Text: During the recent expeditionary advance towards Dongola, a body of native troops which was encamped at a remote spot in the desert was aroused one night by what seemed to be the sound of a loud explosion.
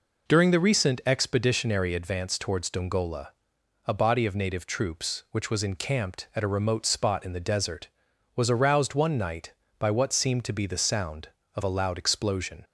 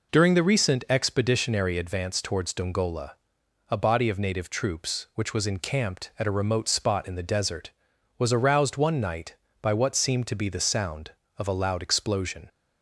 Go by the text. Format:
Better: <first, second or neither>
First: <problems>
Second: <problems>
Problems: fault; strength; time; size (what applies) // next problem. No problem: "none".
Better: neither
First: none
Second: none